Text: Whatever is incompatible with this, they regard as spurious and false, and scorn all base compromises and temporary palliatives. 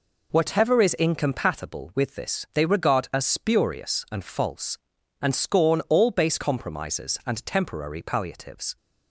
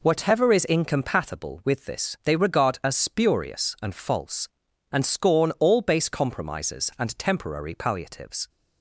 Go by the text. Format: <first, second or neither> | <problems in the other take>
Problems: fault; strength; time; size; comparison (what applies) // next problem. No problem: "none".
neither | none